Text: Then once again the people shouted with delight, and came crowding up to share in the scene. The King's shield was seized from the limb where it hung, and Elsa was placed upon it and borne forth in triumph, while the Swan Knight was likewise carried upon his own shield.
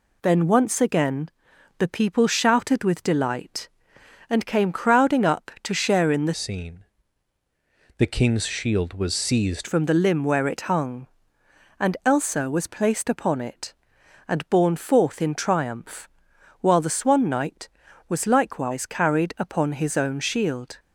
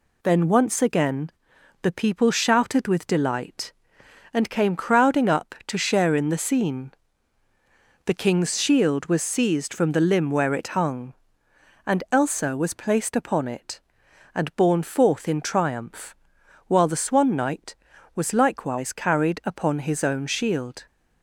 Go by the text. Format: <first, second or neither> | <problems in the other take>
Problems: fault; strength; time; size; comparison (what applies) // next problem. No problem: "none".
second | pauses between "again" and "the"; noticeable; at 1.2 s; 0.48 s long; noticeable in the second // changes voice from "scene" to "seized"; from 6.3 to 9.6 s; 3.3 s long